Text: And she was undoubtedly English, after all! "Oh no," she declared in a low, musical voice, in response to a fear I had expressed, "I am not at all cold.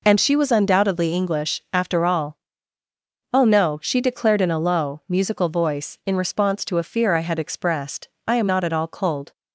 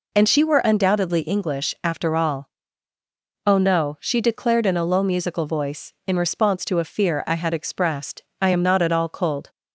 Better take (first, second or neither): first